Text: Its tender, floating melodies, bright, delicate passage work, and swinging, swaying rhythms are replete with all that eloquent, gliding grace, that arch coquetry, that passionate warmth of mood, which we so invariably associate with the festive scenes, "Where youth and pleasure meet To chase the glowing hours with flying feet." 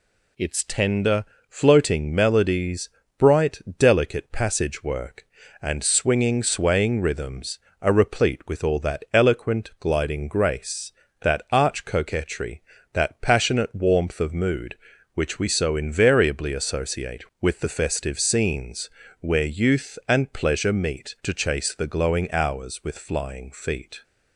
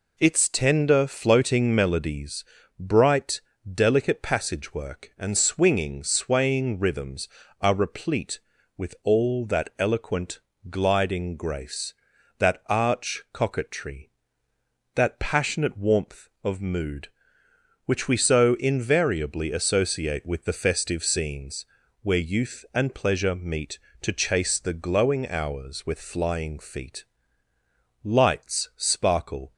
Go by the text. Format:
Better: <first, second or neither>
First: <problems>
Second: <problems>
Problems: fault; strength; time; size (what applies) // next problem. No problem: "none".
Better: first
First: none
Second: goes on to say "Lights sparkle"; from 28.0 s on; 1.5 s long